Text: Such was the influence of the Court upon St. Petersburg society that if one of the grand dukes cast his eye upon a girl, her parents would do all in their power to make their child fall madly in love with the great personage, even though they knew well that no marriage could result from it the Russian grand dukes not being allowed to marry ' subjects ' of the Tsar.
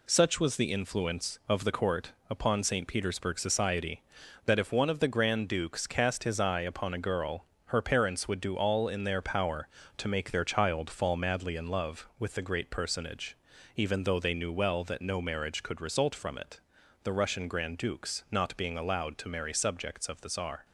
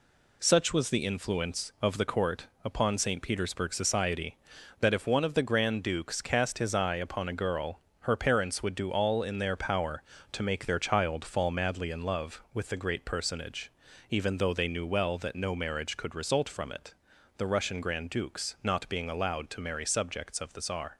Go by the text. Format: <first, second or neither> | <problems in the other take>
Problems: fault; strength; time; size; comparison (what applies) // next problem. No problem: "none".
neither | pauses between "Court" and "upon"; slight; the same in both // pauses between "it" and "the"; the same in both